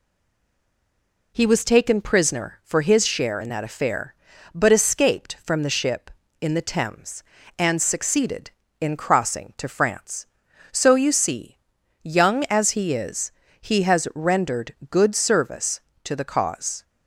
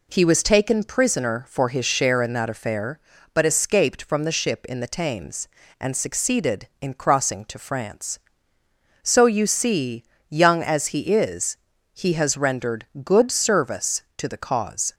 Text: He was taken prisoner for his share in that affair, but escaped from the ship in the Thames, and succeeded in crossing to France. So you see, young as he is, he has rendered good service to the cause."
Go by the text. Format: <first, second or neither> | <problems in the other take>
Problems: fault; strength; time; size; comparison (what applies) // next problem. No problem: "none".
second | stays silent before the first word; noticeable; until 1.3 s; 1.3 s long // pauses between "rendered" and "good"; slight; at 14.7 s; 0.16 s long; slight in the second